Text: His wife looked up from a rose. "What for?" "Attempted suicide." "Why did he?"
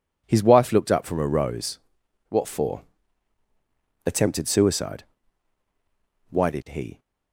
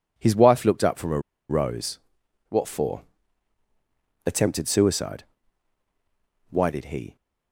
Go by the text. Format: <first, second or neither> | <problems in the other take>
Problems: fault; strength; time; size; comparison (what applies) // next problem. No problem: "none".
first | pauses between "a" and "rose"; slight; at 1.1 s; 0.29 s long